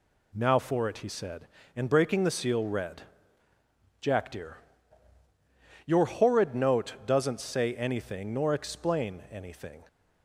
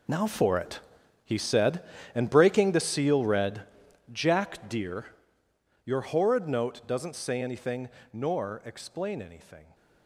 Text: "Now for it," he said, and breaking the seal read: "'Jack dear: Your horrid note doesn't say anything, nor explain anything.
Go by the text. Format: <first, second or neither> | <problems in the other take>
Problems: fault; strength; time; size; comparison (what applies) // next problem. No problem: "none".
first | gets quieter; strong; throughout; 14.5 dB